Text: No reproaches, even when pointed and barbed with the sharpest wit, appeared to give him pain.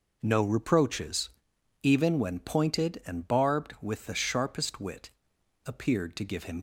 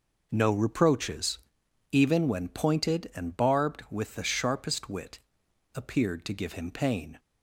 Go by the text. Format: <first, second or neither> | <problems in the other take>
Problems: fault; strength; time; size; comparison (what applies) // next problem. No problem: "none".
second | stops before "pain"; at 6.5 s